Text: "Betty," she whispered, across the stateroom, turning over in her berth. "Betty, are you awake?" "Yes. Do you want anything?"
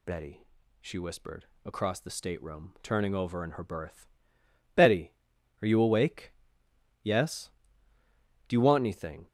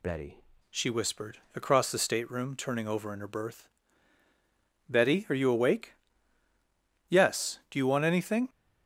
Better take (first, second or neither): first